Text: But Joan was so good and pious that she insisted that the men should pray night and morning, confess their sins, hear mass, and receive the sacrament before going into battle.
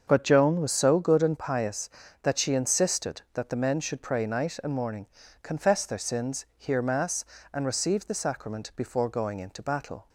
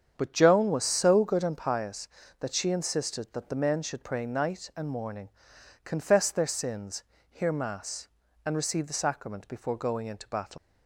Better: first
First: starts louder than the rest; until 1.0 s; 6.5 dB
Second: starts louder than the rest; strong; until 1.1 s; 8 dB // leaves "battle" unfinished; at 10.5 s; 170 ms

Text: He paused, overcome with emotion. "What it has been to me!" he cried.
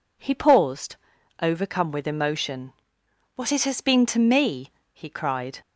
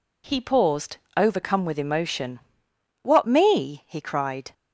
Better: first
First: none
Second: skips "it has been to"; at 3.2 s

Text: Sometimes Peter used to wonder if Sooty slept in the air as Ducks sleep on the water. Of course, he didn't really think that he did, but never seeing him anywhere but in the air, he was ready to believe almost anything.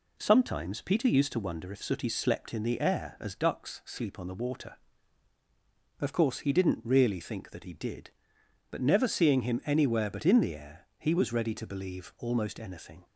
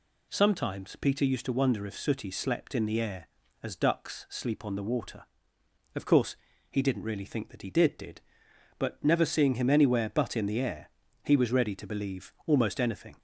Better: first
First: none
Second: says "did" twice; at 7.9 s

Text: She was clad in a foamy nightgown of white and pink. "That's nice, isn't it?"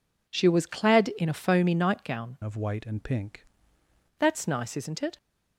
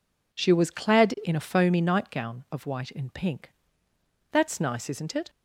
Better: second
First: changes voice from "of" to "pink"; from 2.4 to 3.4 s; 1.0 s long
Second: none

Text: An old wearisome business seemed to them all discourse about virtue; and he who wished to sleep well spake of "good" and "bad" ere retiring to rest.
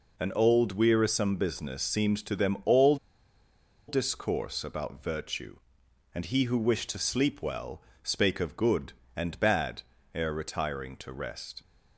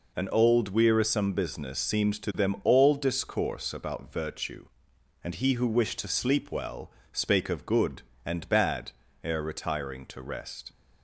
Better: second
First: pauses between "all" and "discourse"; noticeable; at 2.9 s; 0.91 s long // pauses between "well" and "spake"; slight; at 7.7 s; 0.22 s long // pauses between "bad" and "ere"; slight; at 9.8 s; 0.32 s long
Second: pauses between "well" and "spake"; slight; at 6.8 s; 0.22 s long // pauses between "bad" and "ere"; slight; at 8.9 s; 0.32 s long

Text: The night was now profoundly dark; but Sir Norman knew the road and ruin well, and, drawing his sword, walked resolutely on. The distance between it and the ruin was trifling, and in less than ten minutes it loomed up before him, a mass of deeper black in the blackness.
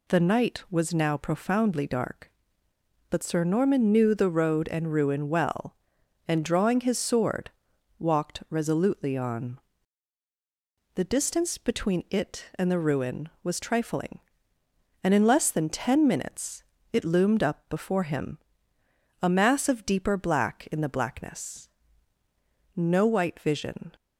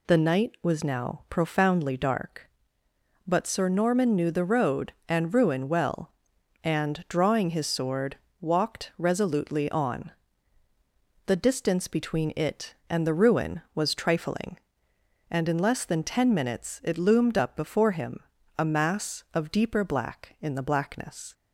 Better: second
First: pauses between "minutes" and "it"; slight; at 16.6 s; 0.28 s long // goes on to say "No white vision"; noticeable; from 22.7 s on; 1.2 s long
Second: none

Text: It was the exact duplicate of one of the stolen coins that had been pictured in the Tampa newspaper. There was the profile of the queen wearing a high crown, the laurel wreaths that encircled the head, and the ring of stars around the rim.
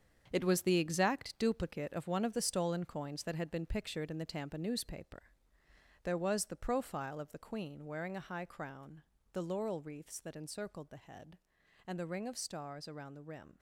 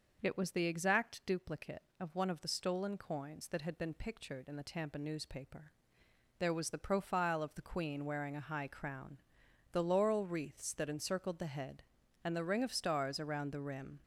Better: second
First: gets quieter; strong; throughout; 9 dB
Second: none

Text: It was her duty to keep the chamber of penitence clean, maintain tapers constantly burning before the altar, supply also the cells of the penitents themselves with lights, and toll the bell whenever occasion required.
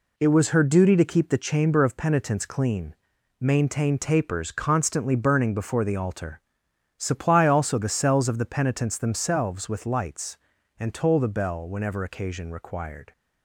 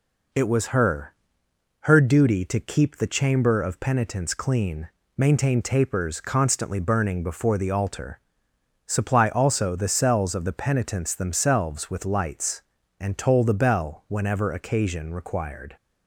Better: first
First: none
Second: says "her" twice; at 1.8 s

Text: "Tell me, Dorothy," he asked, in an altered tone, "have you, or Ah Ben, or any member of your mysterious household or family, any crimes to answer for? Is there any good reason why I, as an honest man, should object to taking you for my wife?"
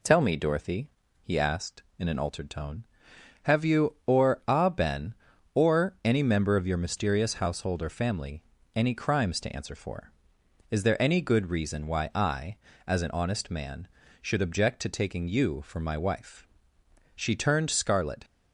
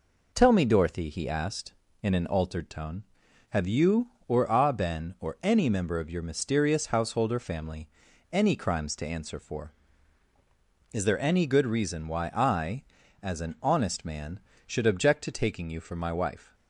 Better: second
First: goes on to say "She turned scarlet"; noticeable; from 17.1 s on; 1.1 s long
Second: none

